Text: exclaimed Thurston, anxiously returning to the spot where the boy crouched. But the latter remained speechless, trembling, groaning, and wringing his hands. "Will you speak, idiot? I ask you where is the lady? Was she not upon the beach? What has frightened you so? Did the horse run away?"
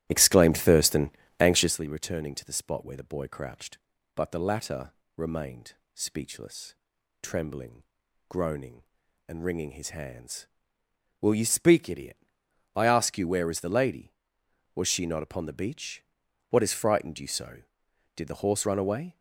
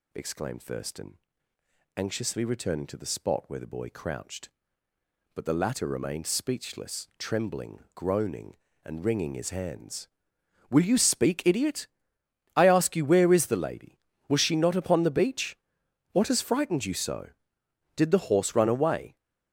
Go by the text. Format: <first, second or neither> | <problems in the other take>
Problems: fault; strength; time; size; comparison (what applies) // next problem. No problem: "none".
second | starts louder than the rest; strong; until 1.9 s; 13 dB // pauses between "latter" and "remained"; slight; at 4.9 s; 0.25 s long // pauses between "remained" and "speechless"; slight; at 5.7 s; 0.22 s long